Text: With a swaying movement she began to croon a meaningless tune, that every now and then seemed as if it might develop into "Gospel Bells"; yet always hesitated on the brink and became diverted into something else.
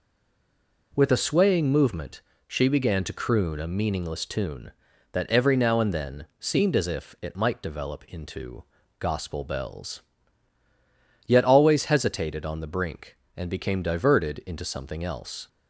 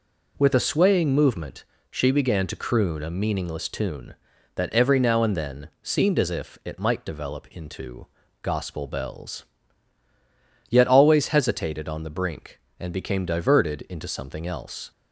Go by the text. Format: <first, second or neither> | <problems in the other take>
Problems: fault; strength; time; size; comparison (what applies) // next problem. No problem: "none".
second | stays silent before the first word; slight; until 0.9 s; 0.9 s long // pauses between "movement" and "she"; slight; at 2.1 s; 0.26 s long; slight in the second // pauses between "into" and "Gospel"; slight; at 8.6 s; 0.36 s long; slight in the second